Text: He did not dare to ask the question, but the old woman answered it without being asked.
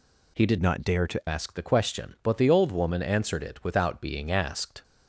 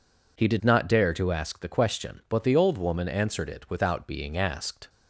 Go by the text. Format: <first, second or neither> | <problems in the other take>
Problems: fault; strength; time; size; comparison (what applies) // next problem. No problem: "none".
second | changes voice from "not" to "to"; from 0.6 to 1.2 s; 0.6 s long